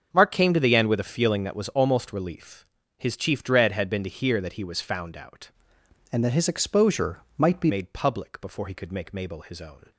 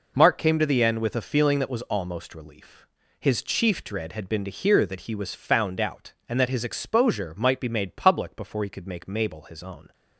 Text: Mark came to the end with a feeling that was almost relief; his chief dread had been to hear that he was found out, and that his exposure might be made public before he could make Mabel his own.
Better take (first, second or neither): second